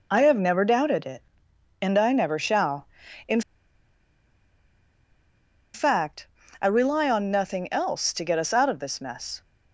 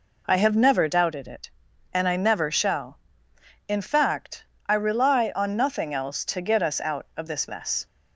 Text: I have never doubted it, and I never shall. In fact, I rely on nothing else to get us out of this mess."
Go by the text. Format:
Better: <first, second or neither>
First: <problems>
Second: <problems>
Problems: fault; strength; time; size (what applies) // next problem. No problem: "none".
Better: second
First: pauses between "In" and "fact"; strong; at 3.4 s; 2.3 s long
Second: none